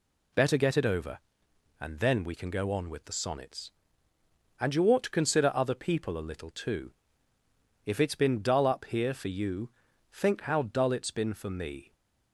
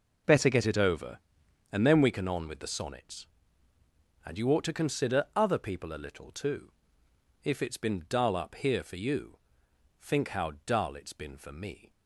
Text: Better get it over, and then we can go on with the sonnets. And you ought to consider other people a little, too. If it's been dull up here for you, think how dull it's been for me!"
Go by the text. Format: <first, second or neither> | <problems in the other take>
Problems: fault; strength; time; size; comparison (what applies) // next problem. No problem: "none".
first | skips "go"; at 2.2 s